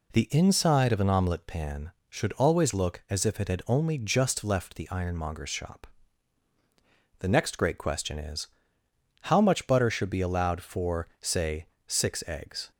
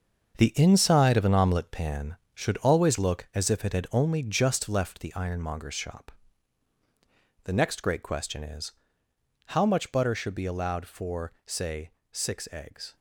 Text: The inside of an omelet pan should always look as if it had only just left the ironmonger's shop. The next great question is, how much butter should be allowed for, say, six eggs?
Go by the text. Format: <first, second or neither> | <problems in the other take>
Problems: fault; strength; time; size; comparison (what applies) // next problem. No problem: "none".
first | gets quieter; strong; throughout; 9 dB